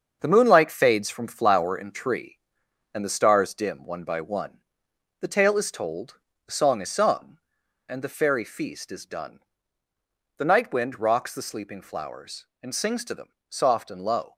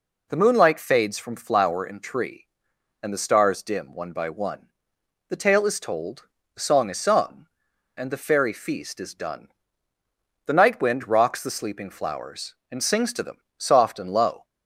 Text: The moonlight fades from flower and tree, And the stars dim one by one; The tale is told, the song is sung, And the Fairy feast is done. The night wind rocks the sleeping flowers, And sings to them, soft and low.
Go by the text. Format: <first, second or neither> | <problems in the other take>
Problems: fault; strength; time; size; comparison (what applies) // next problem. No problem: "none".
second | gets quieter; strong; throughout; 7 dB